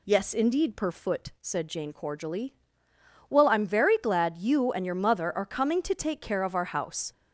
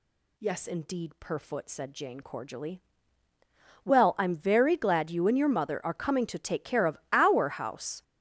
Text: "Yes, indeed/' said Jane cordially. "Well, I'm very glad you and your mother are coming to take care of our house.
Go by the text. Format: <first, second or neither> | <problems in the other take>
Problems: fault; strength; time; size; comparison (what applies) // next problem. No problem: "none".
first | gets louder; strong; throughout; 13 dB